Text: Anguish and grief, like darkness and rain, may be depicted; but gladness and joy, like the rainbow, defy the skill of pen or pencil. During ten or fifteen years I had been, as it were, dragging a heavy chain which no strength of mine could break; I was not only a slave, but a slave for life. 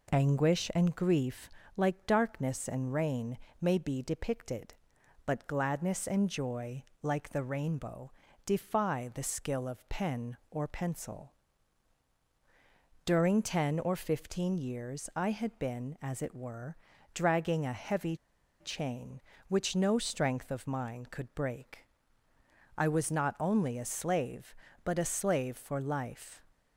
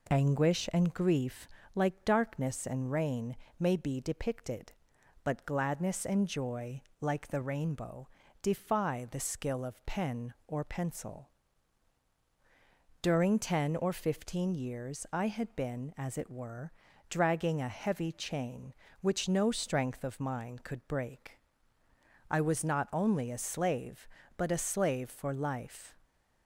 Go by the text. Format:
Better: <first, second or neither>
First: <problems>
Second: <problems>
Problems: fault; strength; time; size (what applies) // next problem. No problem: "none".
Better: second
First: pauses between "heavy" and "chain"; at 18.1 s; 0.43 s long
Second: none